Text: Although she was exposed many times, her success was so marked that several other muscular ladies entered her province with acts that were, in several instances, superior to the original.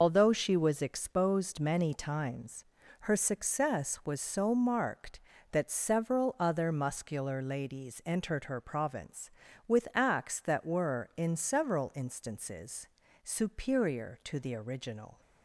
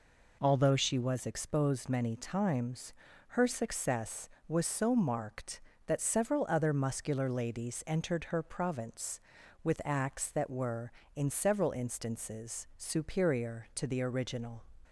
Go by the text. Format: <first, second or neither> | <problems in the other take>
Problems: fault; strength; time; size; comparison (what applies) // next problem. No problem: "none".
second | loses the start of "Although"; at 0.0 s; 85 ms